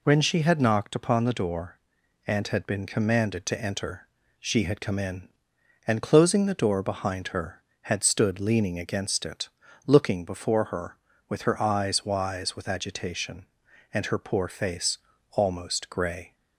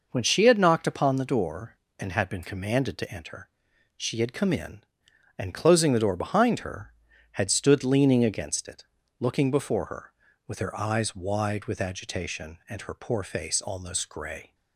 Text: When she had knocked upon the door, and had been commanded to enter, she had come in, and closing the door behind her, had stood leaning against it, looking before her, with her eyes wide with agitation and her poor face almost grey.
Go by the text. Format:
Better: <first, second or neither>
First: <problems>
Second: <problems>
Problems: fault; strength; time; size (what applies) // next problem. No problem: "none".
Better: second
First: says "wise" for "wide"; at 12.0 s // pauses between "face" and "almost"; slight; at 14.9 s; 0.36 s long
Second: none